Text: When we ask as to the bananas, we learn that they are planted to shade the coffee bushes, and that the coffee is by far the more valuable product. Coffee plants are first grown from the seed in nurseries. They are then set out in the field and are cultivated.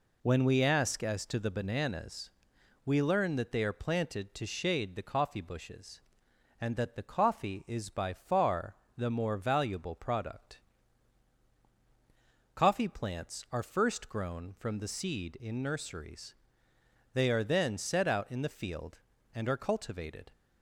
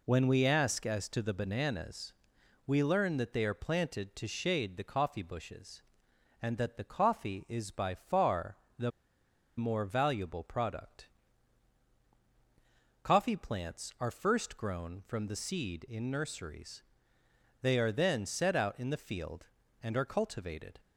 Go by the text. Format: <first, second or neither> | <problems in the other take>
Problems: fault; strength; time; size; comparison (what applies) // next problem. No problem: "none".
first | pauses between "far" and "the"; slight; at 8.5 s; 0.20 s long; slight in the first // pauses between "the" and "more"; noticeable; at 8.9 s; 0.67 s long